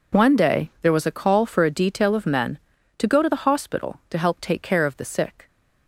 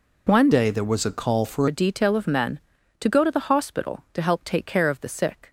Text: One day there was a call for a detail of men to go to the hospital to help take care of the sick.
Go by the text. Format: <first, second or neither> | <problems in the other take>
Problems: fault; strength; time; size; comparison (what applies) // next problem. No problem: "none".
first | changes voice from "day" to "for"; from 0.5 to 1.6 s; 1.1 s long